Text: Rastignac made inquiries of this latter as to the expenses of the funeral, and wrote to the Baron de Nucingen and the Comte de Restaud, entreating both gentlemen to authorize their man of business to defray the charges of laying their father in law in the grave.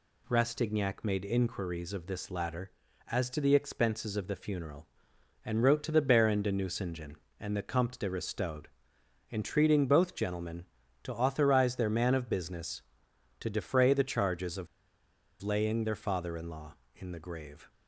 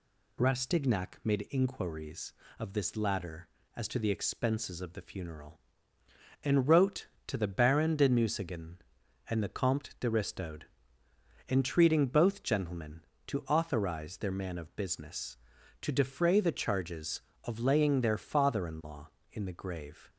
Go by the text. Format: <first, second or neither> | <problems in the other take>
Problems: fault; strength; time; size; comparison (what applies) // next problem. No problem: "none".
second | pauses between "of" and "laying"; noticeable; at 14.6 s; 0.75 s long